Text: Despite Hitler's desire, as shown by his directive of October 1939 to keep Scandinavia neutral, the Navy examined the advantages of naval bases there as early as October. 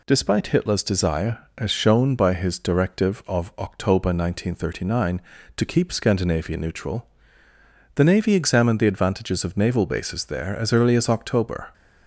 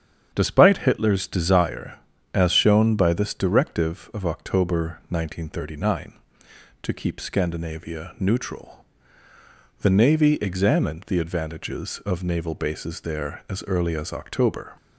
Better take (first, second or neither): first